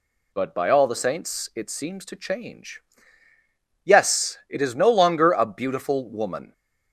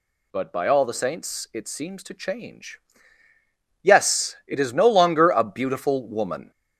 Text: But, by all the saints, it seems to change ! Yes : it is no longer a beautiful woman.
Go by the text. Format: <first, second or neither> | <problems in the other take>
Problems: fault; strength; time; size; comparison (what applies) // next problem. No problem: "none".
first | gets louder; noticeable; throughout; 4.5 dB